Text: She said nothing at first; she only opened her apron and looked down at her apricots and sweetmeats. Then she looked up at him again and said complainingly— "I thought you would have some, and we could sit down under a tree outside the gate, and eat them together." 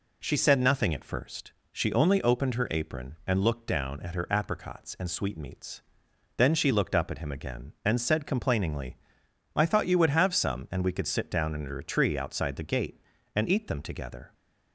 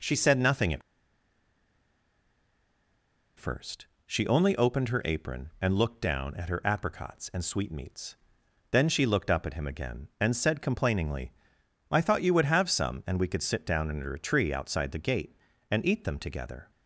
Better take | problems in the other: first | pauses between "at" and "first"; strong; at 0.8 s; 2.5 s long

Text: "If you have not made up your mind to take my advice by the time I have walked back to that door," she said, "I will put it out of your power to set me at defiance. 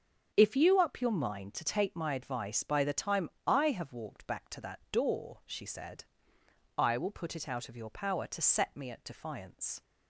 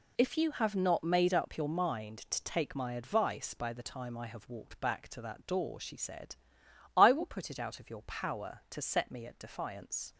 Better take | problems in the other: second | starts louder than the rest; until 1.3 s; 7 dB // skips "have not made"; at 0.7 s // pauses between "time" and "I"; slight; at 3.2 s; 0.18 s long

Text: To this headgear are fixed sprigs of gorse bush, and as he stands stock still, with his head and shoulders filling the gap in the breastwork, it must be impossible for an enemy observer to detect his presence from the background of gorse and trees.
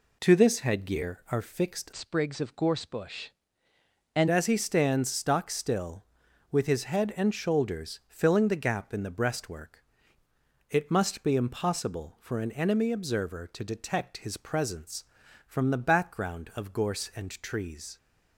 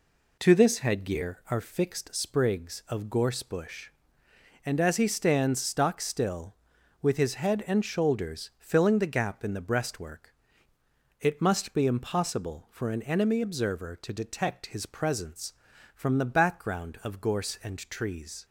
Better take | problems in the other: second | changes voice from "sprigs" to "and"; from 1.9 to 4.2 s; 2.3 s long

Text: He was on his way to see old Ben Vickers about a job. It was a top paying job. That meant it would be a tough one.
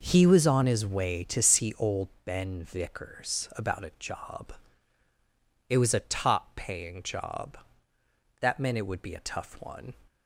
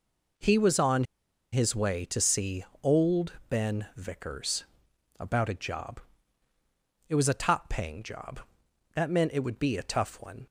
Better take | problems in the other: first | pauses between "on" and "his"; noticeable; at 1.0 s; 0.47 s long // pauses between "see" and "old"; slight; at 2.6 s; 0.18 s long // pauses between "old" and "Ben"; slight; at 3.3 s; 0.16 s long; slight in the first // pauses between "Vickers" and "about"; noticeable; at 4.6 s; 0.54 s long

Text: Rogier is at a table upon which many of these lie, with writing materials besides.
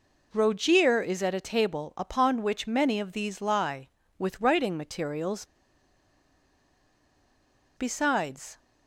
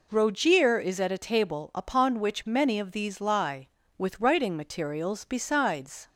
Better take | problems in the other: second | pauses between "materials" and "besides"; strong; at 5.4 s; 2.3 s long

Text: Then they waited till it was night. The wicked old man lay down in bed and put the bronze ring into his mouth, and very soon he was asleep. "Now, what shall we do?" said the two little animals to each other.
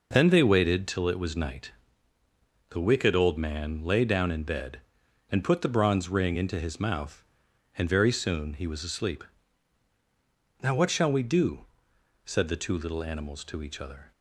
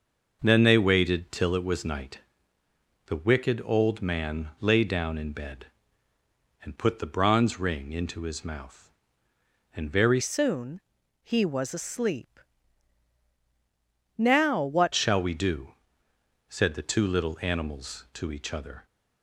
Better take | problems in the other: first | changes voice from "soon" to "what"; from 10.1 to 14.9 s; 4.8 s long // pauses between "soon" and "he"; at 10.8 s; 0.42 s long

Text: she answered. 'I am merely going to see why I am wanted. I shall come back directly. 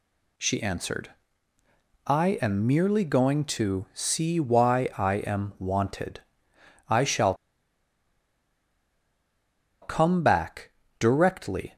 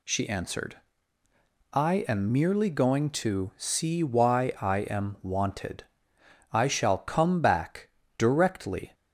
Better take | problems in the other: second | pauses between "shall" and "come"; strong; at 7.3 s; 2.4 s long // pauses between "back" and "directly"; slight; at 10.7 s; 0.28 s long; slight in the second

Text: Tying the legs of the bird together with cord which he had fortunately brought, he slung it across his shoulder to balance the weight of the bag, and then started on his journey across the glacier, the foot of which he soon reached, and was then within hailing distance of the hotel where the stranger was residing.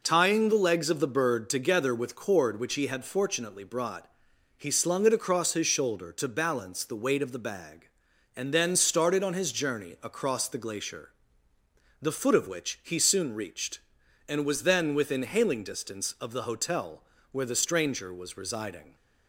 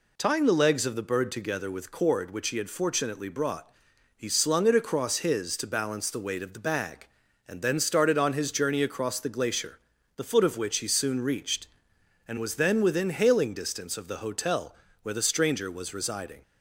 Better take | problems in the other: first | skips "shoulder"; at 5.5 s // pauses between "hotel" and "where"; slight; at 14.7 s; 0.26 s long; slight in the first

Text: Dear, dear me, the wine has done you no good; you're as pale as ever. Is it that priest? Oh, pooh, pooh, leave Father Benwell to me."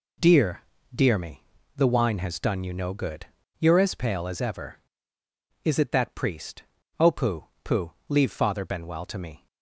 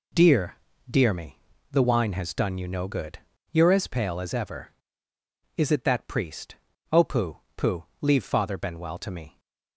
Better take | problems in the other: neither | none

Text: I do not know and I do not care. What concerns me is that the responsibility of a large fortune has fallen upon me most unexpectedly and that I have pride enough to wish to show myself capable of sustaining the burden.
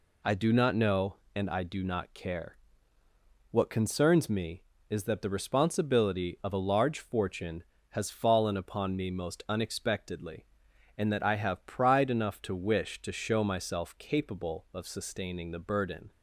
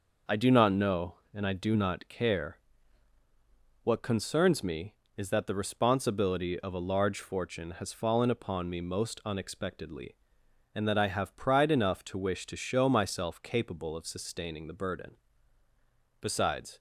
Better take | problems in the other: first | goes on to say "Besides"; from 16.2 s on; 0.56 s long

